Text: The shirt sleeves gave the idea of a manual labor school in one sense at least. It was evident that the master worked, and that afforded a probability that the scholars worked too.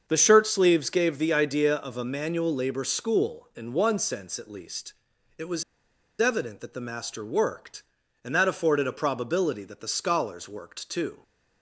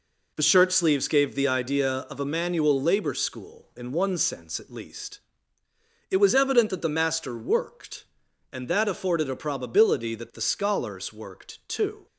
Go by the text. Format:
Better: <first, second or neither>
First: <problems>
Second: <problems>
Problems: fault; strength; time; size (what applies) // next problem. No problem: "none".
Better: second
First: starts louder than the rest; until 1.0 s; 7 dB // pauses between "was" and "evident"; noticeable; at 5.6 s; 0.57 s long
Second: none